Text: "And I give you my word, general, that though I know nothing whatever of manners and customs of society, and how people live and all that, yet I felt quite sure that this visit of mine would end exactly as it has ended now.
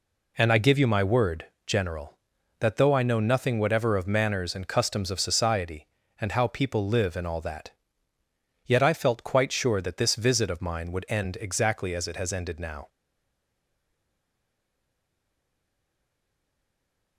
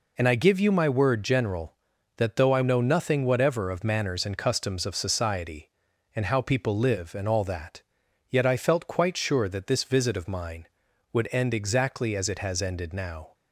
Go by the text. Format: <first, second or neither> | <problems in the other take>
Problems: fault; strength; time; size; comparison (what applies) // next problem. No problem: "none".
second | stays silent after the last word; strong; from 12.8 s on; 4.3 s long